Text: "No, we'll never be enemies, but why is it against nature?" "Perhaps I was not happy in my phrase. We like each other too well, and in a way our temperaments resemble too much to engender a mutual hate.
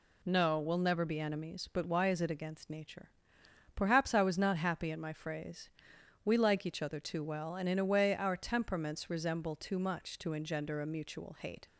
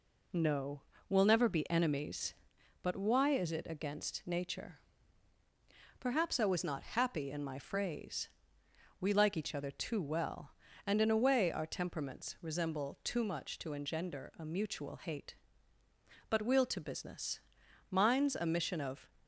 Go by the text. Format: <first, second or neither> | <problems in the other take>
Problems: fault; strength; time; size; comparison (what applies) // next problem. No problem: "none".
first | goes on to say "But we'll to business Mine's a mission of"; strong; from 16.2 s on; 2.8 s long